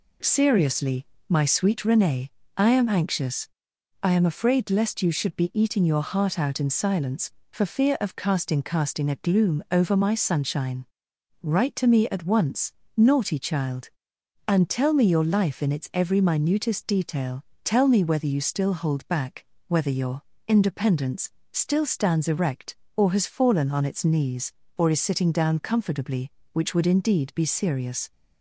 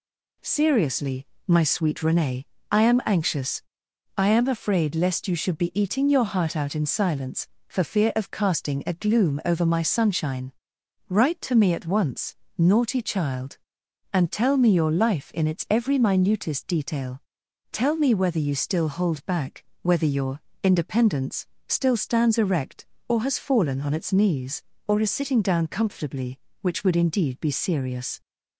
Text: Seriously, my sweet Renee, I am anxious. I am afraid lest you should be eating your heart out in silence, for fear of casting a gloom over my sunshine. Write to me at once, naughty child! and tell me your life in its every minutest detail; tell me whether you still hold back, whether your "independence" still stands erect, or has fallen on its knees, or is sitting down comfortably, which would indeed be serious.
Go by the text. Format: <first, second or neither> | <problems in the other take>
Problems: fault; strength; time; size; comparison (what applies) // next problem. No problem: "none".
second | says "casting" twice; at 8.6 s // pauses between "your" and "independence"; slight; at 20.2 s; 0.26 s long; slight in the second // pauses between "independence" and "still"; slight; at 21.3 s; 0.20 s long; slight in the second